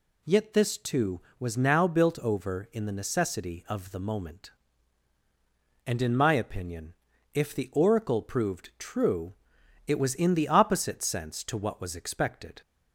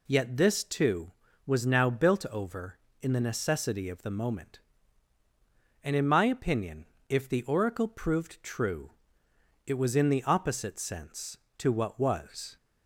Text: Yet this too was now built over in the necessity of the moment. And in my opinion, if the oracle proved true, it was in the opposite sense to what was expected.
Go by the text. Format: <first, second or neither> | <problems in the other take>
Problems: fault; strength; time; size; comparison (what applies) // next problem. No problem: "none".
first | stops before "expected"; at 12.5 s